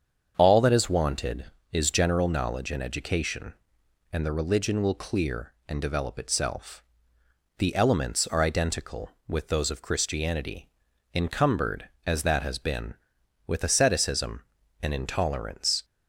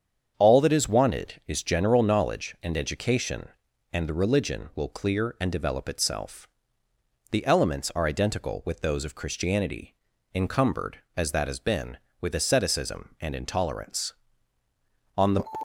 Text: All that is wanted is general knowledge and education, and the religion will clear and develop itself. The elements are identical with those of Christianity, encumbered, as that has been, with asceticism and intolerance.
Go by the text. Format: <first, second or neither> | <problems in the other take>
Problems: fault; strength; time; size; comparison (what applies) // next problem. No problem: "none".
first | starts louder than the rest; strong; until 1.3 s; 7.5 dB; strong in the first // goes on to say "On the"; slight; from 15.1 s on; 0.28 s long